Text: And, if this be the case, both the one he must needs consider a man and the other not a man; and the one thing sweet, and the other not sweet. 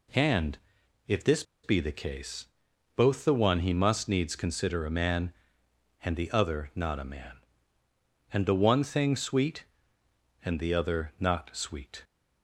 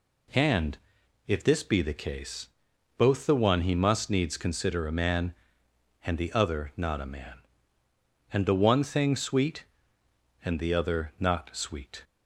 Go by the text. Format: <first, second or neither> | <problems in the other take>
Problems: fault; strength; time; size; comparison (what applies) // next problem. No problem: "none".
second | pauses between "this" and "be"; slight; at 1.4 s; 0.20 s long